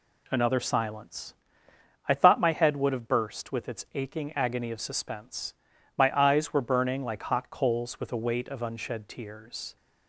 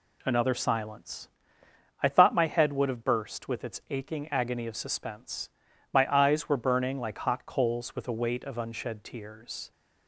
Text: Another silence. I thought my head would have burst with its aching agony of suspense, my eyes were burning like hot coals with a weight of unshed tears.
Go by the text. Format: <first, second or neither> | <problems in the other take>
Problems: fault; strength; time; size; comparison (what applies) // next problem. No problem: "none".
neither | none